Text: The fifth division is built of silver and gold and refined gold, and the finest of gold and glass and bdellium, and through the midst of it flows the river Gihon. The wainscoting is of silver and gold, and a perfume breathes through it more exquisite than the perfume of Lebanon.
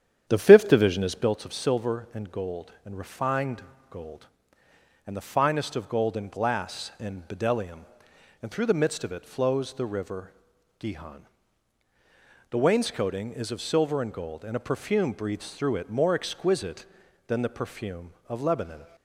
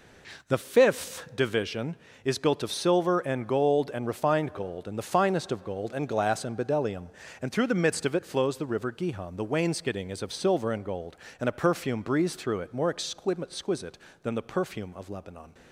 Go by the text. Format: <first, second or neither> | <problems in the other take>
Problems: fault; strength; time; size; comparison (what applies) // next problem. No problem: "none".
second | starts louder than the rest; strong; until 1.4 s; 9.5 dB // pauses between "refined" and "gold"; slight; at 3.6 s; 0.28 s long // pauses between "river" and "Gihon"; noticeable; at 10.3 s; 0.48 s long